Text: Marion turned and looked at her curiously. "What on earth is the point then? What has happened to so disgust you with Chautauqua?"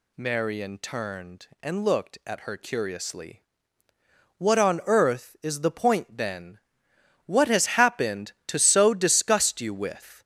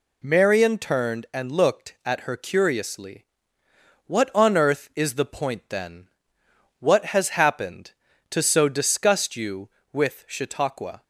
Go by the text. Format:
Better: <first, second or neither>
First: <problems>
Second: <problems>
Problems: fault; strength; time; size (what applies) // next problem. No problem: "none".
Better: second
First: stops before "Chautauqua"; at 10.2 s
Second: none